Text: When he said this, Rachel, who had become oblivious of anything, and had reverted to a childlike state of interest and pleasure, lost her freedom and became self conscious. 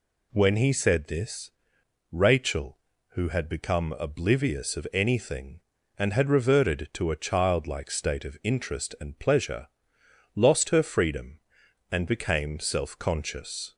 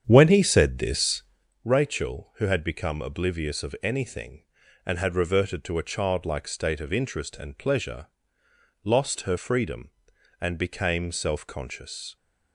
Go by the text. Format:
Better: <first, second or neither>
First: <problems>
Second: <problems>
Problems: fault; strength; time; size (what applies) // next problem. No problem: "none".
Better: first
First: none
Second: starts louder than the rest; strong; until 1.5 s; 8.5 dB